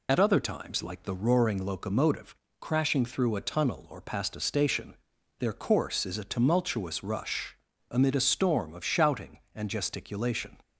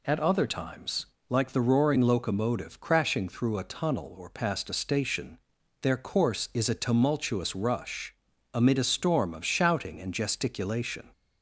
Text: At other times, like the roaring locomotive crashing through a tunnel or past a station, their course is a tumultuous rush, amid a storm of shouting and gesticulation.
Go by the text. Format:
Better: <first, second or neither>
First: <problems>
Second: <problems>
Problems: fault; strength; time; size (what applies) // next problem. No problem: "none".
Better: second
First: loses the start of "At"; at 0.0 s; 55 ms // pauses between "locomotive" and "crashing"; slight; at 2.3 s; 0.26 s long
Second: none